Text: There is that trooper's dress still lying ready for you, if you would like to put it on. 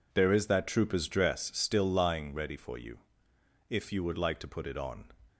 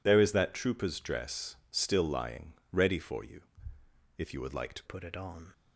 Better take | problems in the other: first | pauses between "dress" and "still"; slight; at 1.5 s; 0.16 s long // pauses between "lying" and "ready"; slight; at 2.5 s; 0.18 s long // changes voice at "put"; from 4.8 s on; 0.7 s long

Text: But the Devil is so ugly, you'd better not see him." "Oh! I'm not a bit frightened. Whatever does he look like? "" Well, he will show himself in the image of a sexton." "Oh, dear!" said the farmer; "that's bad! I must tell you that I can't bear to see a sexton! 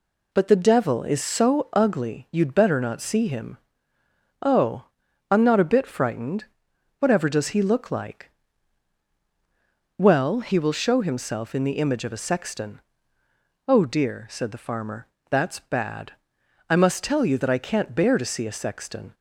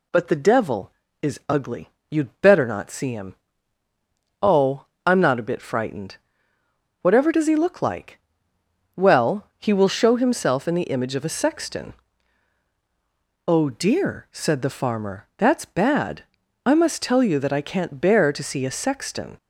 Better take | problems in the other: first | skips "so"; at 1.4 s

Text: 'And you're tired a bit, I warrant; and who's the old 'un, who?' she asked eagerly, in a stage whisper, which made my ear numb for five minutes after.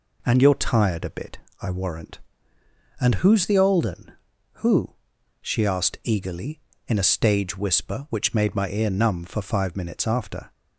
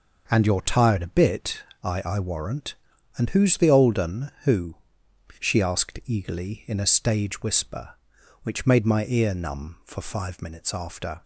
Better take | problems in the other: first | says "I" twice; at 2.0 s

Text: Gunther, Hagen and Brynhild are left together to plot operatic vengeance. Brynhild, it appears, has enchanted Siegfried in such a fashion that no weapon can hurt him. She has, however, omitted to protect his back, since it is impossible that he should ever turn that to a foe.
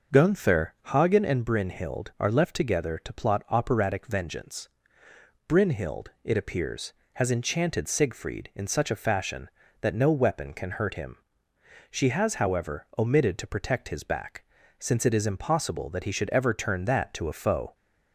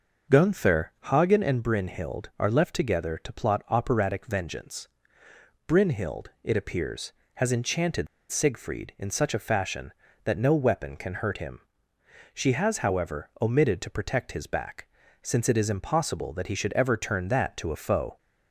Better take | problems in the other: first | starts louder than the rest; noticeable; until 1.4 s; 6 dB; noticeable in the first // pauses between "enchanted" and "Siegfried"; slight; at 8.0 s; 0.22 s long

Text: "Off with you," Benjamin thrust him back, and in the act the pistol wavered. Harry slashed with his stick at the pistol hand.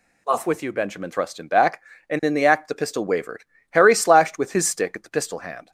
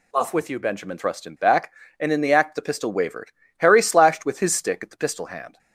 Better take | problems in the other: neither | none

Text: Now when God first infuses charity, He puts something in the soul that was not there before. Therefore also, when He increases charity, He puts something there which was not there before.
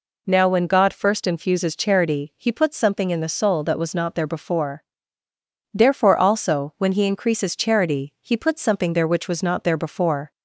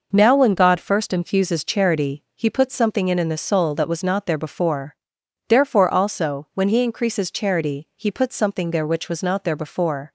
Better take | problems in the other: first | says "in" twice; at 3.1 s

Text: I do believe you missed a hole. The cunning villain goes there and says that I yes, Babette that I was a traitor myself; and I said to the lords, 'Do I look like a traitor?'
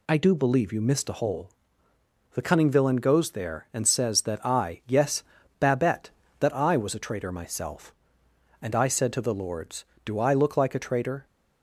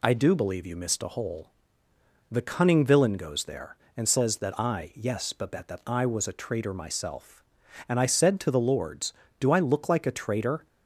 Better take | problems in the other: neither | none

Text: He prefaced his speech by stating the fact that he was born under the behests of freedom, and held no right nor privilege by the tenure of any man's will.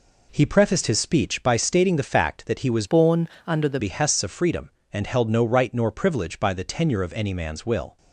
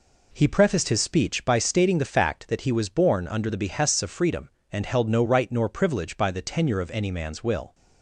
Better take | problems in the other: second | changes voice from "born" to "the"; from 2.8 to 3.7 s; 0.9 s long // pauses between "born" and "under"; slight; at 3.2 s; 0.16 s long

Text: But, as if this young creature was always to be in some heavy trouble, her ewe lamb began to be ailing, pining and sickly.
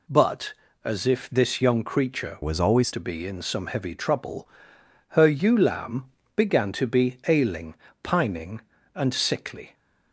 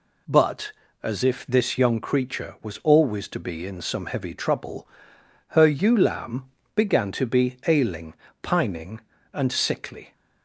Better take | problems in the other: second | changes voice from "was" to "always"; from 2.4 to 2.9 s; 0.5 s long // pauses between "lamb" and "began"; slight; at 6.0 s; 0.30 s long; slight in the second

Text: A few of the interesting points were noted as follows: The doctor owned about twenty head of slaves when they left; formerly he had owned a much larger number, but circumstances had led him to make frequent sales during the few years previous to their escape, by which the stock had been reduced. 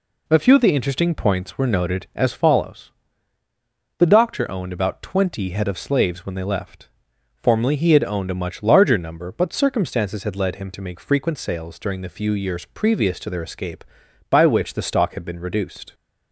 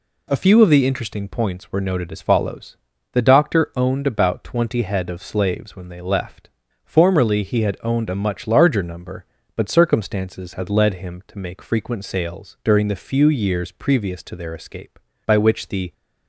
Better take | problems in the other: first | stops before "stock had been reduced"; at 15.9 s

